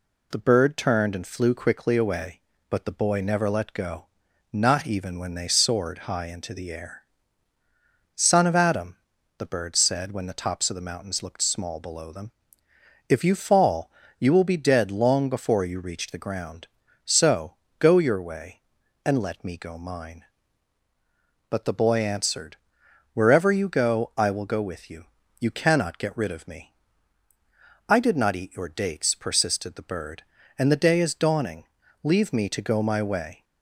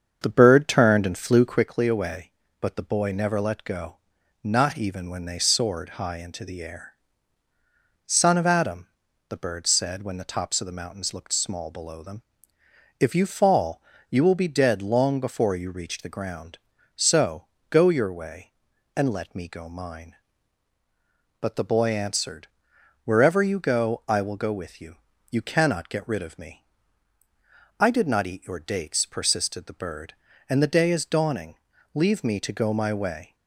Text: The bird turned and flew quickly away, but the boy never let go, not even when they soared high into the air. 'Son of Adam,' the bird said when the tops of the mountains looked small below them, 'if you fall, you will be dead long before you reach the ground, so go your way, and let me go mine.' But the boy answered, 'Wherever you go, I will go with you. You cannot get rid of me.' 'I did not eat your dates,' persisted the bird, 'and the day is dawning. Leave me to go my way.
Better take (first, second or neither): first